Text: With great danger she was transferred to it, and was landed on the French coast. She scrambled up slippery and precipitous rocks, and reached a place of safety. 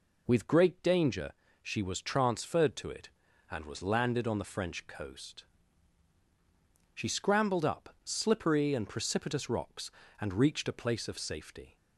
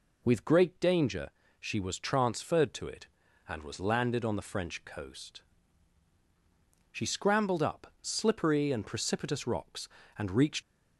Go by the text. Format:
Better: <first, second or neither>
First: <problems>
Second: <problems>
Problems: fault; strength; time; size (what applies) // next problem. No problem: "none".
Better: first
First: pauses between "danger" and "she"; slight; at 1.3 s; 0.28 s long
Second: pauses between "danger" and "she"; slight; at 1.3 s; 0.28 s long // stops before "a place of safety"; at 10.6 s